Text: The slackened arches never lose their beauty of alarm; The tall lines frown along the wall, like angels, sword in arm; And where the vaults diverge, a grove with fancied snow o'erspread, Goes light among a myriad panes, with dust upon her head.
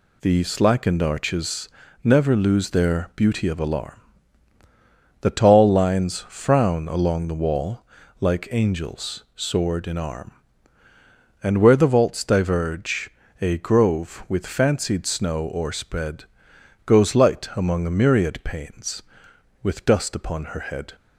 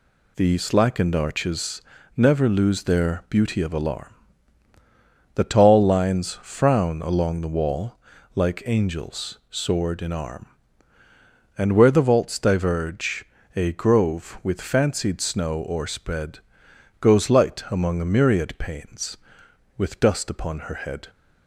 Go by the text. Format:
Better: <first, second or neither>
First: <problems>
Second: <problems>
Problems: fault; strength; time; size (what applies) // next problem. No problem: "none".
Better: neither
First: pauses between "arches" and "never"; slight; at 1.6 s; 0.34 s long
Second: pauses between "arches" and "never"; slight; at 1.8 s; 0.34 s long